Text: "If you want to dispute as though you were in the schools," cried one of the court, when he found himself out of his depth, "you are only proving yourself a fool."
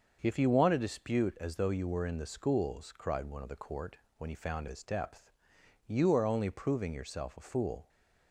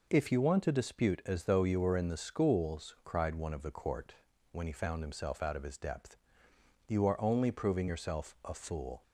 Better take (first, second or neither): second